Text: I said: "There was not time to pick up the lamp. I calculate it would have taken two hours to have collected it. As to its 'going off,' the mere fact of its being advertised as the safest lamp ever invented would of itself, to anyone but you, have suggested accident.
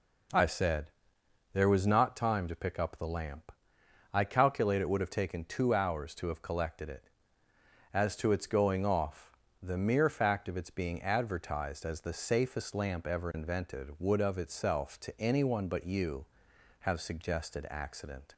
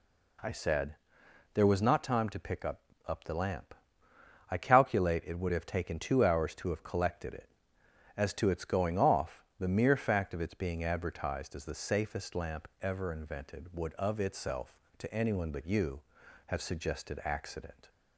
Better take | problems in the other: first | says "up" twice; at 3.0 s

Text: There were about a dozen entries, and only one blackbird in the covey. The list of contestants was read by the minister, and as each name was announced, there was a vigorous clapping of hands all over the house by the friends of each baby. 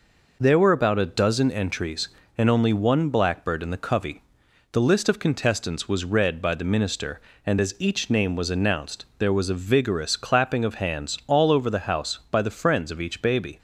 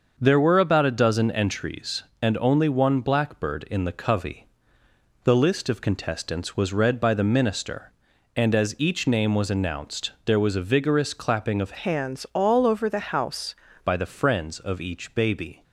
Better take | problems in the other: first | starts louder than the rest; until 1.2 s; 6.5 dB // changes voice from "hands" to "house"; from 11.7 to 13.5 s; 1.8 s long

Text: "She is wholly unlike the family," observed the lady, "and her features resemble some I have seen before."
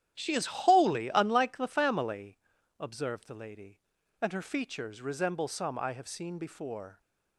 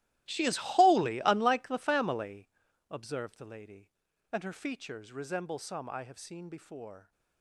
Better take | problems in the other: first | gets quieter; strong; throughout; 18.5 dB // starts louder than the rest; strong; until 1.3 s; 15.5 dB; strong in the first

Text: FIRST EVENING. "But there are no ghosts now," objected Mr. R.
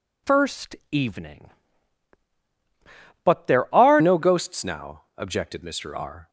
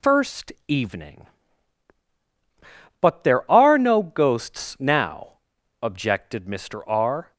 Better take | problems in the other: second | pauses between "FIRST" and "EVENING"; slight; at 0.7 s; 0.16 s long; slight in the second // changes voice at "no"; from 4.0 s on; 2.2 s long

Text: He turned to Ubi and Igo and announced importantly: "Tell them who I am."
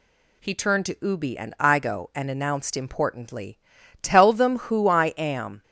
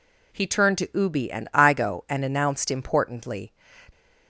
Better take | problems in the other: first | stops before "Tell them who I am"; at 3.9 s

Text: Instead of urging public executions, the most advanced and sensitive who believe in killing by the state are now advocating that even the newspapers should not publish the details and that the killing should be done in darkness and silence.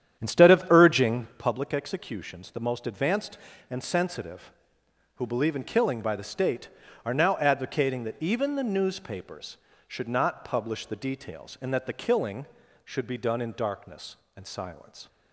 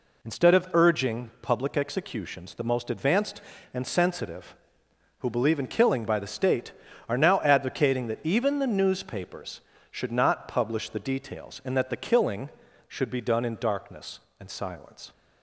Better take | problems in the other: second | starts louder than the rest; strong; until 1.5 s; 9.5 dB

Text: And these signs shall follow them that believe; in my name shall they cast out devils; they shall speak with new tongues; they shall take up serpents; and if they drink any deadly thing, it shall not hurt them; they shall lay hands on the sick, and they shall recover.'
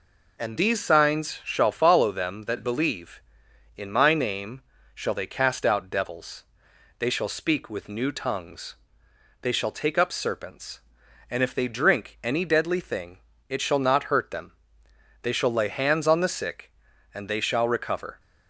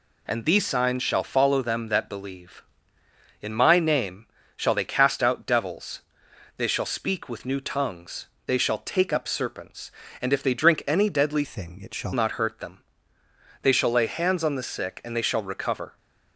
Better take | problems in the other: first | pauses between "name" and "shall"; slight; at 4.2 s; 0.30 s long; slight in the first // changes voice from "thing" to "shall"; from 11.4 to 12.1 s; 0.7 s long

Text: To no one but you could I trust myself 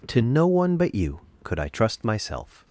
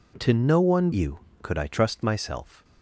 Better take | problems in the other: first | skips "but"; at 0.9 s

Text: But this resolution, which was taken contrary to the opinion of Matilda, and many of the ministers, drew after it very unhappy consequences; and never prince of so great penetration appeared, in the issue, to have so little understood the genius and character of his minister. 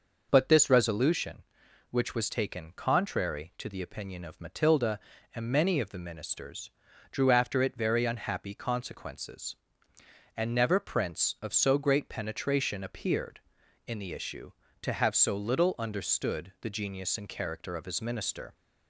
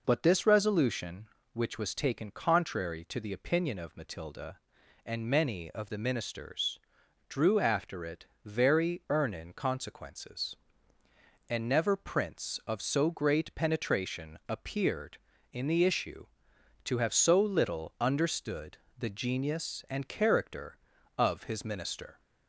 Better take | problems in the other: first | pauses between "it" and "very"; slight; at 8.2 s; 0.18 s long // says "earnin" for "unhappy"; at 9.0 s // pauses between "understood" and "the"; slight; at 18.7 s; 0.18 s long

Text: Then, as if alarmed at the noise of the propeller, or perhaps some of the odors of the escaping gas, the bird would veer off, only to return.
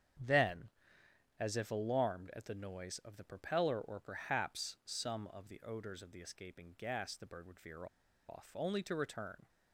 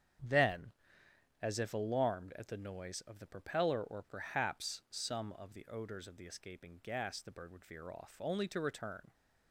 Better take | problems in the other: second | starts louder than the rest; strong; until 1.9 s; 8.5 dB; strong in the second // pauses between "veer" and "off"; at 7.8 s; 0.42 s long

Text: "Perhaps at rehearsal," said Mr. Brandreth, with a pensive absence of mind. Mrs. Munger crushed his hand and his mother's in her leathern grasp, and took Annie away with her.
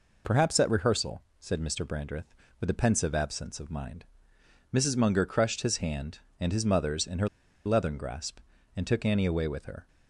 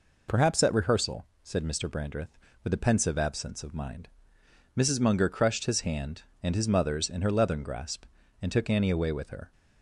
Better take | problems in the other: second | pauses between "her" and "leathern"; at 7.2 s; 0.37 s long

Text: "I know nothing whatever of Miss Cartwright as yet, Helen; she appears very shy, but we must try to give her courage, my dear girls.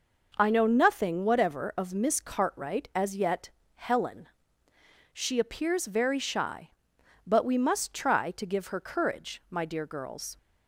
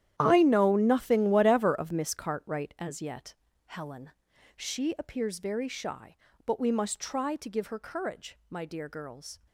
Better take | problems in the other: first | gets quieter; strong; throughout; 15 dB

